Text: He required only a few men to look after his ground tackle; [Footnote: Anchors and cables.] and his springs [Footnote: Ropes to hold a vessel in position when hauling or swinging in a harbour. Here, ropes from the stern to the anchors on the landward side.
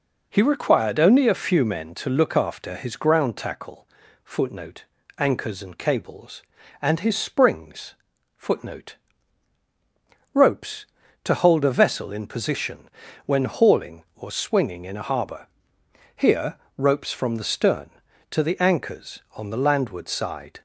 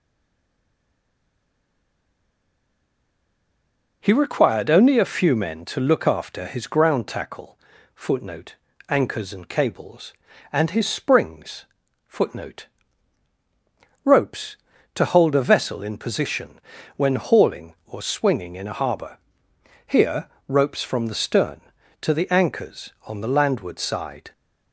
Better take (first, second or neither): first